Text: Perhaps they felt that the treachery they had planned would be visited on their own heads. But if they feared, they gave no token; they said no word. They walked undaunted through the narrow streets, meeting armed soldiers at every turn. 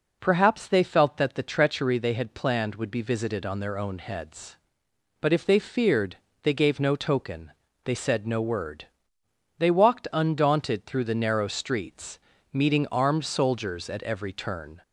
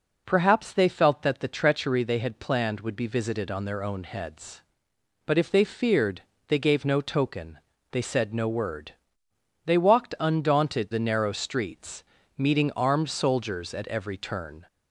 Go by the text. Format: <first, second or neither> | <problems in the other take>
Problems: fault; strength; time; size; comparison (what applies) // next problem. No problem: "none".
first | skips "through"; at 10.9 s